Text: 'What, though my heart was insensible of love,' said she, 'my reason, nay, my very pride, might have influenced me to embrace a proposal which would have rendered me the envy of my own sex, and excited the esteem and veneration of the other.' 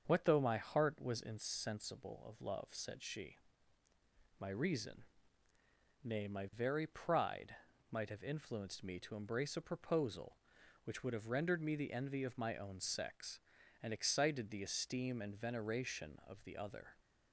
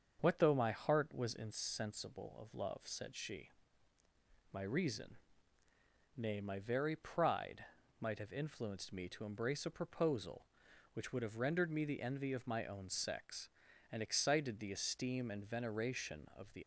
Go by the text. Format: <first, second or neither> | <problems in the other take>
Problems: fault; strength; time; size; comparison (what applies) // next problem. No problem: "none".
first | starts louder than the rest; until 1.2 s; 7 dB; also in the first // stops before "other"; at 16.6 s